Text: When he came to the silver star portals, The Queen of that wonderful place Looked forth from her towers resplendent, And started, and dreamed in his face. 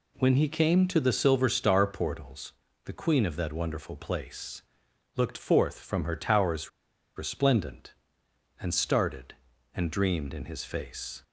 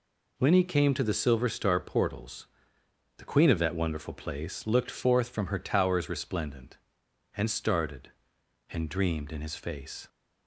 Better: second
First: pauses between "place" and "Looked"; noticeable; at 4.6 s; 0.54 s long // pauses between "towers" and "resplendent"; noticeable; at 6.6 s; 0.47 s long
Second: none

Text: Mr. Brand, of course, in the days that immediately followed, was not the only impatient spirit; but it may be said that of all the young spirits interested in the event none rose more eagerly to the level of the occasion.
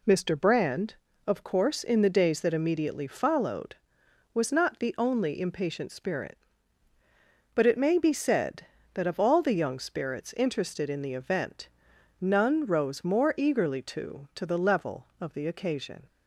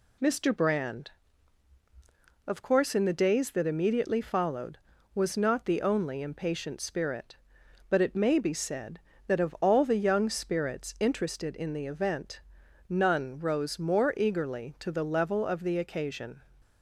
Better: second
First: pauses between "event" and "none"; noticeable; at 11.6 s; 0.52 s long // says "to" twice; at 14.3 s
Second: pauses between "event" and "none"; noticeable; at 12.3 s; 0.50 s long

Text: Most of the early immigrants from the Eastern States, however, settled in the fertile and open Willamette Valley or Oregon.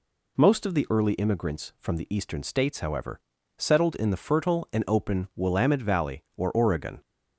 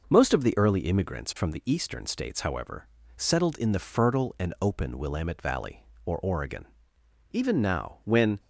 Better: first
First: none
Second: goes on to say "Even now when"; noticeable; from 7.3 s on; 1.0 s long

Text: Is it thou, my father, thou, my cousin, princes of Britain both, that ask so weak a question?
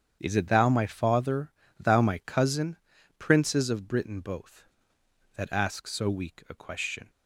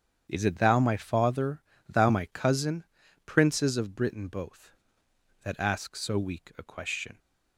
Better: neither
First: starts louder than the rest; strong; until 1.2 s; 8 dB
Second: starts louder than the rest; strong; until 1.3 s; 8 dB

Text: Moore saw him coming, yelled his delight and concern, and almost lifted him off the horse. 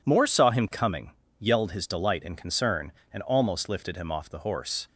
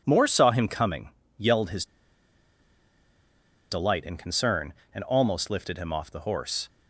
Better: first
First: none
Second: pauses between "his" and "delight"; strong; at 1.8 s; 1.8 s long

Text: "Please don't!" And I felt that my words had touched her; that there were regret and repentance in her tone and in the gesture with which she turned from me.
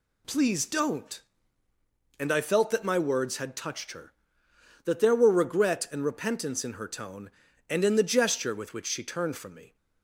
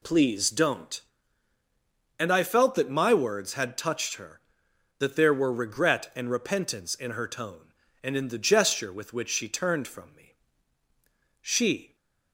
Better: first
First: none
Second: goes on to say "She"; from 11.4 s on; 0.54 s long

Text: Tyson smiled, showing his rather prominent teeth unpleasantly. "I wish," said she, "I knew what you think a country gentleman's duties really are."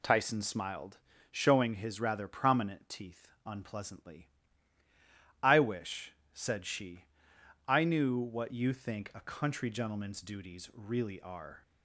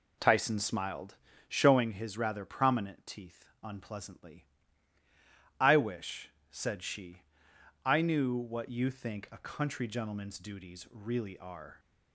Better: first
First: pauses between "teeth" and "unpleasantly"; slight; at 3.2 s; 0.18 s long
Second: starts louder than the rest; until 1.9 s; 3.5 dB // pauses between "teeth" and "unpleasantly"; slight; at 3.4 s; 0.18 s long

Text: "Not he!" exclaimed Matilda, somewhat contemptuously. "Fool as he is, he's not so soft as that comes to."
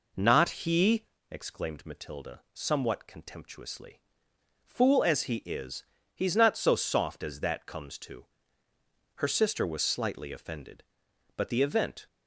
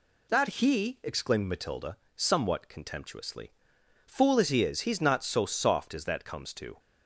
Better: second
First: goes on to say "Her sister was slightly offended but the event"; strong; from 9.1 s on; 2.9 s long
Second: none

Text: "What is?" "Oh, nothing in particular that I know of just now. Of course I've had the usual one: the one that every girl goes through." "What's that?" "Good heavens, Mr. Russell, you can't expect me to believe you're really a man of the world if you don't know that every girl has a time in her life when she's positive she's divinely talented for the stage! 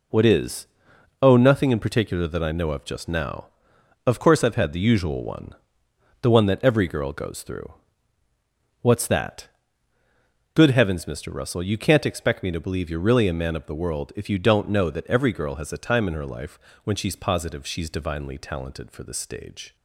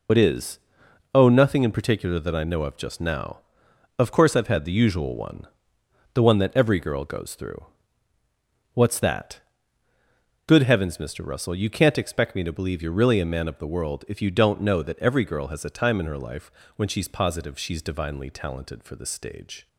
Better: first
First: pauses between "life" and "when"; slight; at 16.5 s; 0.24 s long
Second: loses the start of "What"; at 0.0 s; 65 ms // pauses between "life" and "when"; slight; at 16.5 s; 0.24 s long

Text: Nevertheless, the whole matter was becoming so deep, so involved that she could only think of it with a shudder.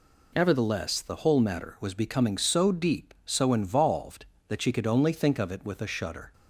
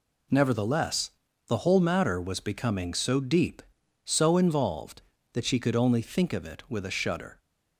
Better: neither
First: none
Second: none

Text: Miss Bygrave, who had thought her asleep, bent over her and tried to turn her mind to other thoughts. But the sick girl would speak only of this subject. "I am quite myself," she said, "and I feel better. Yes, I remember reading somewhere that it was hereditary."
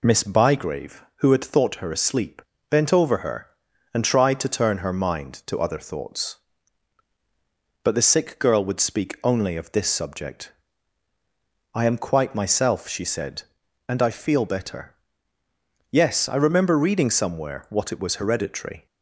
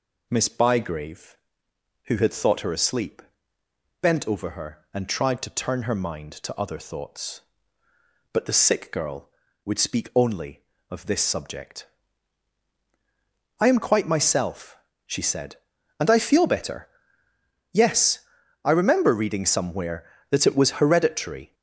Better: second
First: says "what" for "that"; at 17.6 s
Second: none

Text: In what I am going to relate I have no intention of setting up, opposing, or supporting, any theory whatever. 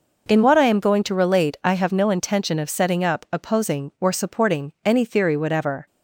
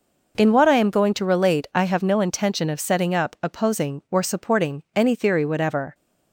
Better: neither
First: none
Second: none

